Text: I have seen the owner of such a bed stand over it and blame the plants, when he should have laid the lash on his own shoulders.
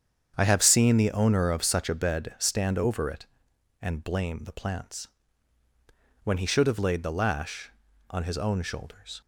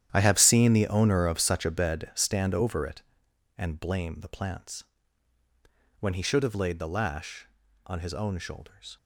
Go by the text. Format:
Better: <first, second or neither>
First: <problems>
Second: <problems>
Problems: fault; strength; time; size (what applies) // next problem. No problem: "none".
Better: first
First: starts louder than the rest; strong; until 1.3 s; 8 dB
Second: gets quieter; strong; throughout; 14 dB // starts louder than the rest; strong; until 1.1 s; 11 dB